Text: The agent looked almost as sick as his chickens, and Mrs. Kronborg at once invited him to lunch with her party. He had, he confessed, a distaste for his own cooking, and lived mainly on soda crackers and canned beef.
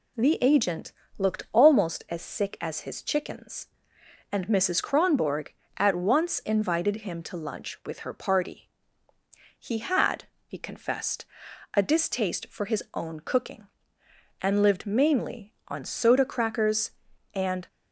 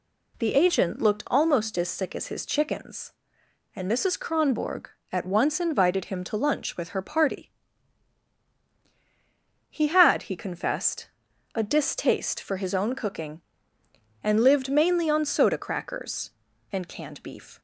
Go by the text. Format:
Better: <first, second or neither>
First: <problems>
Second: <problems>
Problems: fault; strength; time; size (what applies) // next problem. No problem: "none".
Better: second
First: pauses between "agent" and "looked"; slight; at 0.9 s; 0.26 s long // stops before "canned beef"; at 17.6 s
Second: none